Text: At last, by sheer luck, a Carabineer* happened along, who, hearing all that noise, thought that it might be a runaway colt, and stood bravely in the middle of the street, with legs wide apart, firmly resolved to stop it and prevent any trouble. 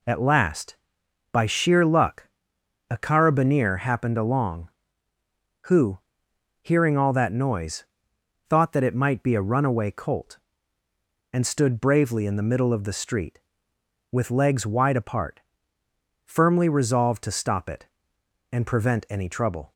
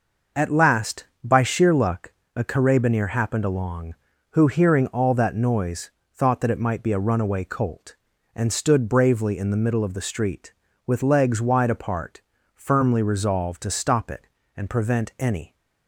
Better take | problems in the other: first | stops before "trouble"; at 15.5 s

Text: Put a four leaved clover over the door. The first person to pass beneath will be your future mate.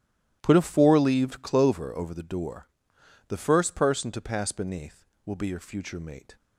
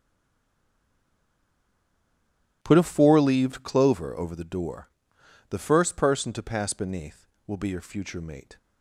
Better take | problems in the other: first | stays silent before the first word; strong; until 2.6 s; 2.6 s long // starts louder than the rest; strong; until 3.6 s; 13 dB; strong in the first

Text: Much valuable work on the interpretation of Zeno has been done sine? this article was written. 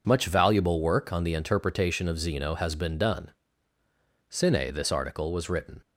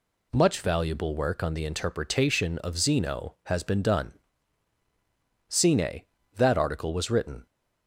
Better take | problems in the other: first | pauses between "done" and "sine"; strong; at 4.1 s; 1.3 s long; noticeable in the first // says "that" for "this"; at 6.3 s

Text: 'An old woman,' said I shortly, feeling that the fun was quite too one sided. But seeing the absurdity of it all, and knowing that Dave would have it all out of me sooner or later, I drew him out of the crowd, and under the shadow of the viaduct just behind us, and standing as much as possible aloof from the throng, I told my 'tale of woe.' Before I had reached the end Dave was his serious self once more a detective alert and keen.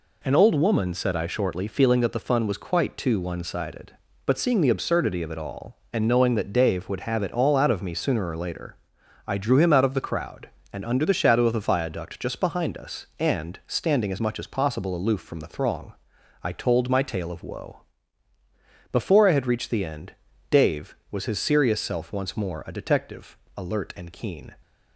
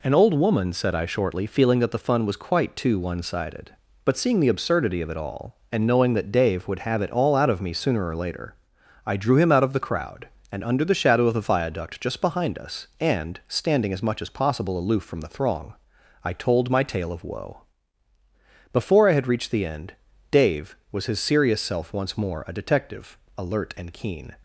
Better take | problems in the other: neither | pauses between "end" and "Dave"; slight; the same in both // pauses between "detective" and "alert"; slight; the same in both

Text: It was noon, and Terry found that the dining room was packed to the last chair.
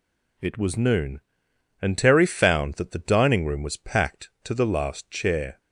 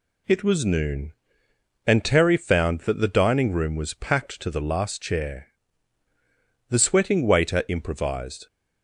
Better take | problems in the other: first | goes on to say "The sweating waiter improvised"; strong; from 6.6 s on; 1.7 s long

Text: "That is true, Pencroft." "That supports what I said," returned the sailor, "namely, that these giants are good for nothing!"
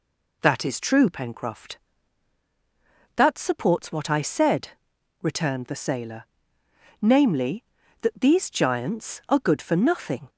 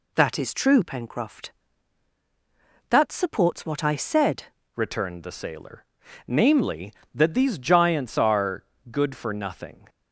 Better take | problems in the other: first | changes voice at "returned"; from 4.7 s on; 5.1 s long // pauses between "are" and "good"; slight; at 8.6 s; 0.26 s long

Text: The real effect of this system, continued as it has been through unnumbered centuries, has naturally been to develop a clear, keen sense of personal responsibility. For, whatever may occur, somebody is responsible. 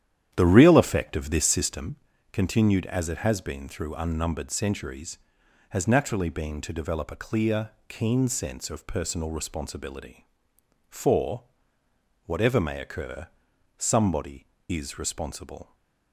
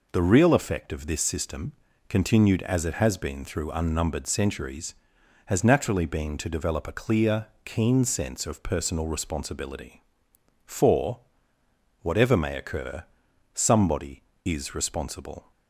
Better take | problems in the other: second | starts louder than the rest; strong; until 1.9 s; 10.5 dB

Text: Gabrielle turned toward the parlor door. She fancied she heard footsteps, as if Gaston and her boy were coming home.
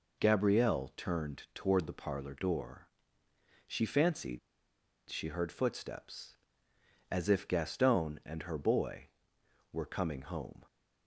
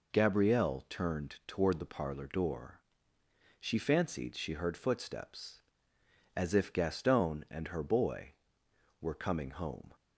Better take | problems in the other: second | pauses between "fancied" and "she"; noticeable; at 4.3 s; 0.69 s long

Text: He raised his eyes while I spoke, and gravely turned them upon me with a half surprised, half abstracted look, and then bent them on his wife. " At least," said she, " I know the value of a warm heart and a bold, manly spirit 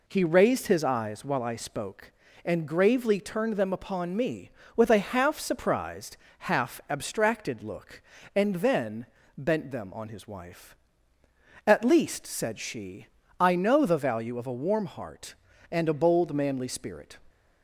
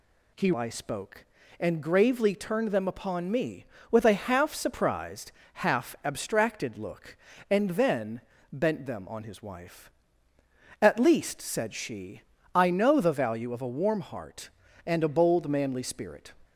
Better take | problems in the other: first | skips "raised his eyes while"; at 0.5 s // pauses between "then" and "bent"; slight; at 8.2 s; 0.30 s long; slight in the first

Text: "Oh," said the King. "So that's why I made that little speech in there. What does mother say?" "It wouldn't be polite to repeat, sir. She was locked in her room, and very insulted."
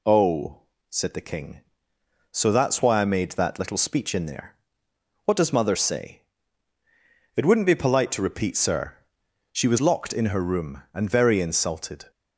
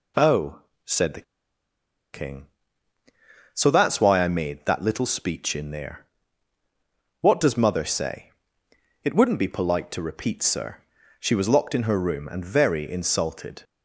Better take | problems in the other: first | pauses between "the" and "King"; noticeable; at 1.2 s; 0.89 s long

